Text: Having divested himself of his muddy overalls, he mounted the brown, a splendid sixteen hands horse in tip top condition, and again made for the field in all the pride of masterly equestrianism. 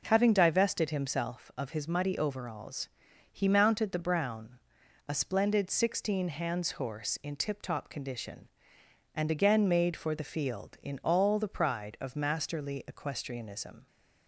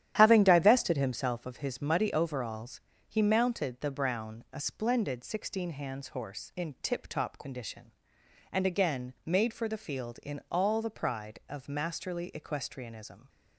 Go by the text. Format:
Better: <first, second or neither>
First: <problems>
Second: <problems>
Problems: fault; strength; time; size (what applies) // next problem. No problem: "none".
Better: first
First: none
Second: starts louder than the rest; strong; until 1.4 s; 11.5 dB